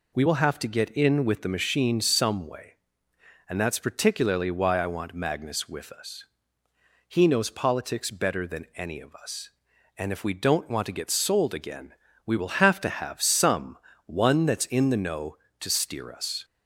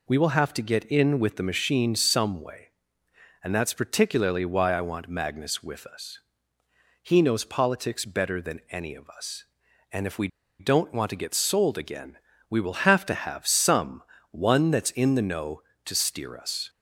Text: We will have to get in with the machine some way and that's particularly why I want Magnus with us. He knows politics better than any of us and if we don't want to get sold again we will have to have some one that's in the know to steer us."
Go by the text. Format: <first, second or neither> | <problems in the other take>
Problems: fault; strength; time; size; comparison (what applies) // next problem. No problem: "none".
first | pauses between "we" and "don't"; slight; at 10.2 s; 0.31 s long // pauses between "again" and "we"; slight; at 12.1 s; 0.32 s long; slight in the first // pauses between "some" and "one"; slight; at 14.0 s; 0.30 s long; slight in the first